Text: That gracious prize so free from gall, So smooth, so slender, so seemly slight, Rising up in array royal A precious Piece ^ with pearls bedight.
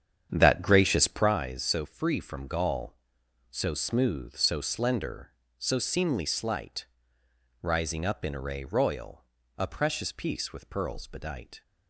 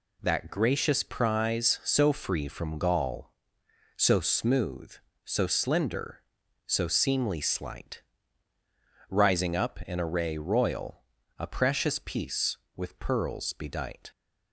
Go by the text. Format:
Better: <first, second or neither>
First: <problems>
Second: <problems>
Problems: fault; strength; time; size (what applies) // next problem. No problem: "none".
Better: second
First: starts louder than the rest; strong; until 1.4 s; 8.5 dB // pauses between "royal" and "A"; slight; at 9.2 s; 0.34 s long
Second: pauses between "royal" and "A"; slight; at 11.0 s; 0.36 s long